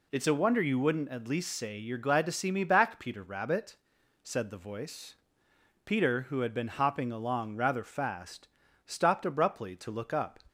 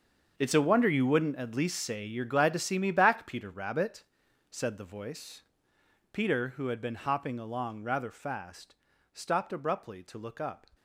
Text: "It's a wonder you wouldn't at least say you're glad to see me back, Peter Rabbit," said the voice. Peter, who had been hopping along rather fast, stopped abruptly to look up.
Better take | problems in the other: first | gets quieter; strong; throughout; 13.5 dB

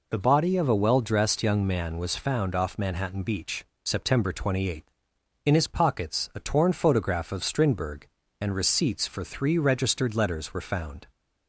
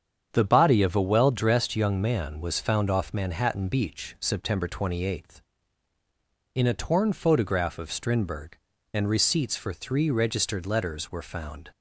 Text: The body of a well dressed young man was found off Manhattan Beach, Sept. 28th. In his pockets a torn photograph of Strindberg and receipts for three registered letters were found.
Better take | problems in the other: first | starts louder than the rest; strong; until 1.3 s; 7.5 dB // skips "his pockets"; at 6.6 s

